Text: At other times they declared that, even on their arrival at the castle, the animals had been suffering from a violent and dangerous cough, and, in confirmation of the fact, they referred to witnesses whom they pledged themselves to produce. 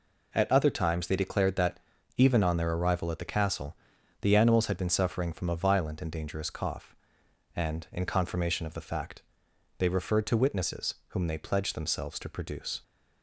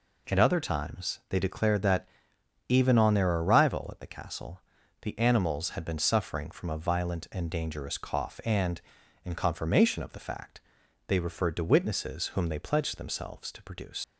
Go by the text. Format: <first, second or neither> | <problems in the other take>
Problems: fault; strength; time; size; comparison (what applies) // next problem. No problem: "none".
first | leaves "produce" unfinished; at 14.0 s; 120 ms